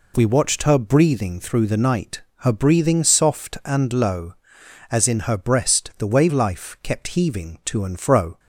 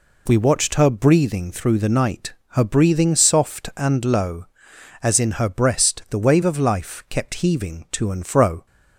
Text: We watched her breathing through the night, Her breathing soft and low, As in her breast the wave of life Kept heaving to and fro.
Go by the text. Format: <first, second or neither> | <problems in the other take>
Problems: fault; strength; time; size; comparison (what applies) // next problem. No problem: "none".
second | skips "of"; at 6.3 s